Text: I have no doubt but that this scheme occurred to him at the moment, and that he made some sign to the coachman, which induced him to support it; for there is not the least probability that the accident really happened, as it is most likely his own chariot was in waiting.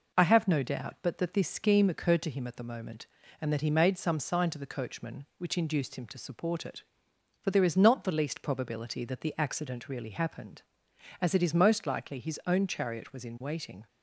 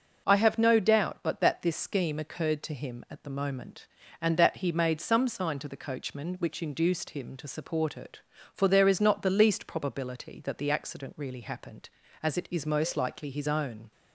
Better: first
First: none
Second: stops before "chariot was in waiting"; at 13.9 s

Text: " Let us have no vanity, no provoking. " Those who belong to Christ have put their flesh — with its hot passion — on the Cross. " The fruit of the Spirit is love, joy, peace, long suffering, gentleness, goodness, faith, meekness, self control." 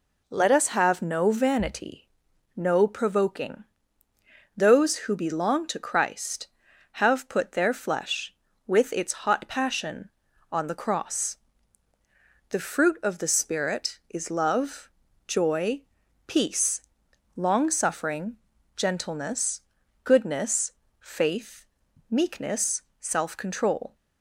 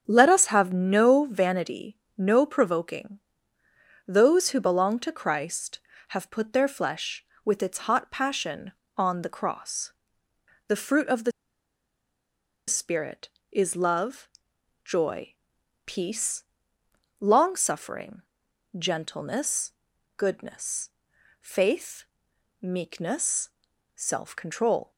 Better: first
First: none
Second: starts louder than the rest; strong; until 1.0 s; 7 dB // pauses between "the" and "Spirit"; strong; at 11.3 s; 1.3 s long

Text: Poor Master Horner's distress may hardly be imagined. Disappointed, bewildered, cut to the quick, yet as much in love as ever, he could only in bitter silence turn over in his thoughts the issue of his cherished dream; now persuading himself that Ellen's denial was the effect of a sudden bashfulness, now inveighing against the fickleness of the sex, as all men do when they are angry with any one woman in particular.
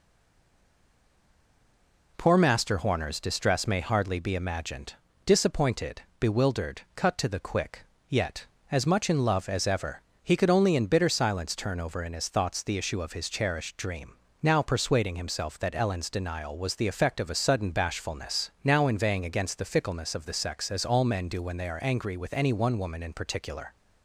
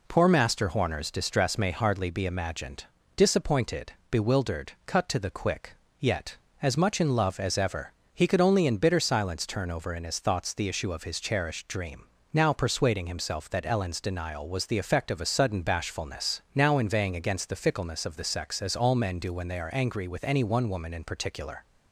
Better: second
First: stays silent before the first word; until 2.1 s; 2.1 s long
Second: none

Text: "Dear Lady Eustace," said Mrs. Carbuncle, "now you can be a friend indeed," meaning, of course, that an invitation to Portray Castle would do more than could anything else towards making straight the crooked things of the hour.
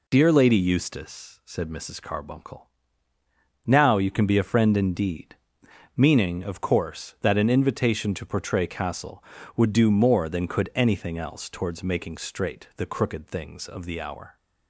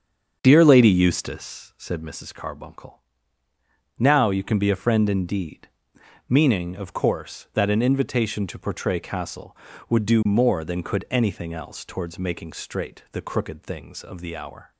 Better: first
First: none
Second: starts louder than the rest; strong; until 2.1 s; 7 dB

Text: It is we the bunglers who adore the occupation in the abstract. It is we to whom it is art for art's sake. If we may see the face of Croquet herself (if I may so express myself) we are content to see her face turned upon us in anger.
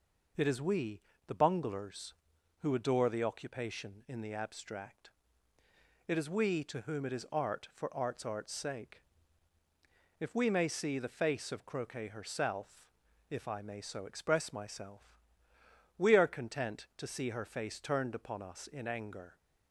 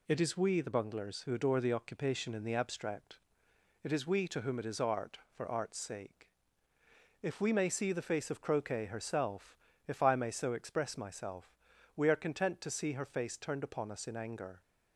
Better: second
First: pauses between "we" and "the"; slight; at 1.0 s; 0.26 s long // says "art's" twice; at 8.2 s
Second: none

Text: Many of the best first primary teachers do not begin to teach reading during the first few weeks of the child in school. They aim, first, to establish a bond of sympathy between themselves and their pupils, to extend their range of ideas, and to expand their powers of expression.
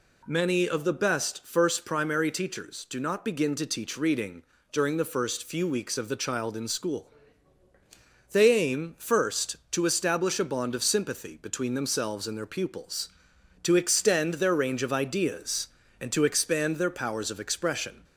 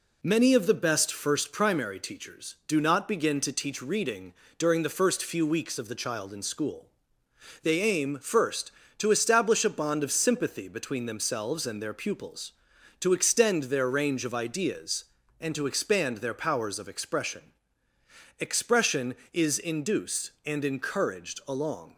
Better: first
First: pauses between "reading" and "during"; slight; at 4.4 s; 0.30 s long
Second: pauses between "reading" and "during"; slight; at 4.3 s; 0.26 s long // goes on to say "Expression is induced and encouraged along"; strong; from 18.3 s on; 3.5 s long

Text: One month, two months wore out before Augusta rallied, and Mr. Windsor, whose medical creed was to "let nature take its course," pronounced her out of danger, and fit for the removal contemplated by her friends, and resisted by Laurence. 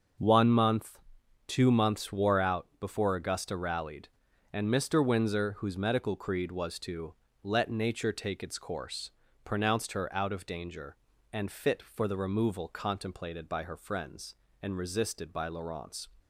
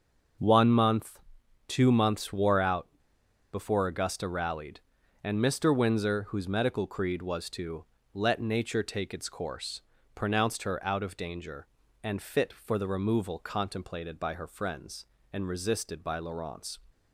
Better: first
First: starts louder than the rest; until 1.6 s; 6.5 dB // pauses between "to" and "let"; slight; at 7.1 s; 0.28 s long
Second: starts louder than the rest; until 1.8 s; 6.5 dB // pauses between "out" and "before"; noticeable; at 2.8 s; 0.65 s long // pauses between "to" and "let"; slight; at 7.8 s; 0.28 s long

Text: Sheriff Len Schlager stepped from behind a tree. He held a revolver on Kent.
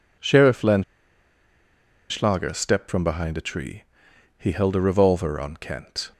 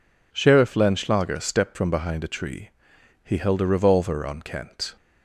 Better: second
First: pauses between "Len" and "Schlager"; strong; at 0.8 s; 1.2 s long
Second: none

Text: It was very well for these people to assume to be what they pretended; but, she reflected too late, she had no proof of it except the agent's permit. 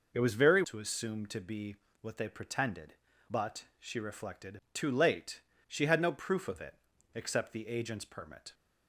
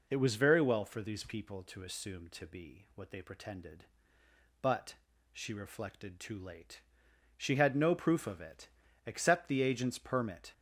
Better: second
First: skips "well for these people"; at 0.6 s // pauses between "be" and "what"; slight; at 1.7 s; 0.26 s long // pauses between "it" and "except"; at 6.7 s; 0.38 s long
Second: pauses between "it" and "except"; slight; at 8.6 s; 0.36 s long

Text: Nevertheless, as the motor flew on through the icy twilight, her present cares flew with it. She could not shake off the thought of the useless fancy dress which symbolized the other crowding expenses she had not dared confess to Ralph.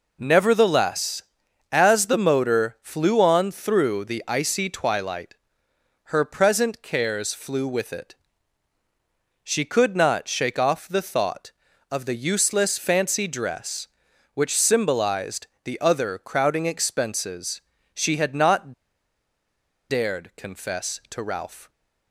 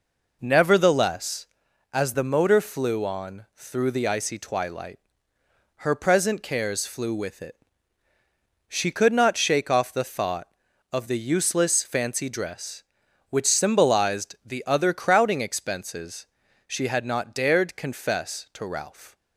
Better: second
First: pauses between "symbolized" and "the"; slight; at 15.4 s; 0.16 s long // pauses between "expenses" and "she"; slight; at 17.6 s; 0.32 s long // pauses between "not" and "dared"; at 18.7 s; 1.1 s long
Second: pauses between "expenses" and "she"; at 16.2 s; 0.40 s long

